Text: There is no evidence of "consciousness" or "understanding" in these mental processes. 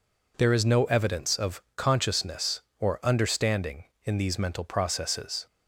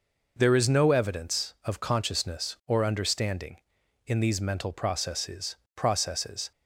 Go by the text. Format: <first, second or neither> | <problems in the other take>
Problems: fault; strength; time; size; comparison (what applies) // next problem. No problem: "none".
first | says "processes" twice; at 5.7 s